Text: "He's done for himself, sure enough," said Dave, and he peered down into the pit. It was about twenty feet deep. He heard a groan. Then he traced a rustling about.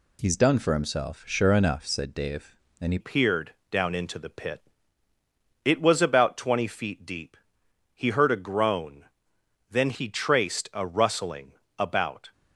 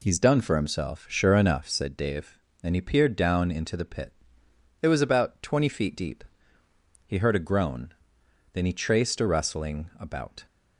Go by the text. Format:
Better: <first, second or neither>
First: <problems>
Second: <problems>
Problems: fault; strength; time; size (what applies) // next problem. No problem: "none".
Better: second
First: changes voice at "peered"; from 3.0 s on; 9.3 s long // pauses between "peered" and "down"; slight; at 3.5 s; 0.16 s long // pauses between "rustling" and "about"; slight; at 11.5 s; 0.24 s long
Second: none